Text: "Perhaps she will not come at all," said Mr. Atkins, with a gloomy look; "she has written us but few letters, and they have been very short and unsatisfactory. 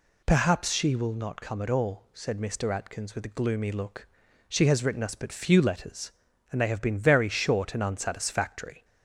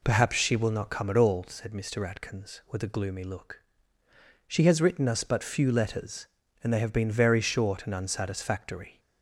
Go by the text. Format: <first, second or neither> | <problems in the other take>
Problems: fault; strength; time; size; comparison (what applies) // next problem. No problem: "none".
first | starts louder than the rest; until 1.4 s; 3.5 dB